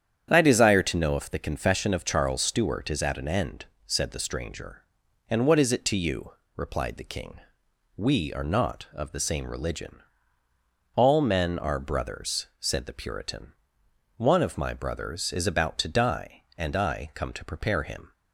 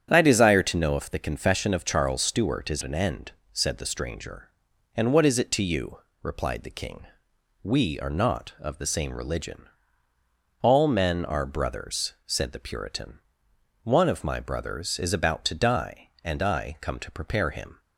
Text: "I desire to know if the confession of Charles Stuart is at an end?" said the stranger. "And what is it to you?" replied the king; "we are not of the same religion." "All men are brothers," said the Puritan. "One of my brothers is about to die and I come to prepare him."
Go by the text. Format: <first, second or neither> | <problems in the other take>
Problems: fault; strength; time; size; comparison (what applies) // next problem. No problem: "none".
first | starts louder than the rest; strong; until 1.1 s; 9 dB; strong in the first // skips "at"; at 2.8 s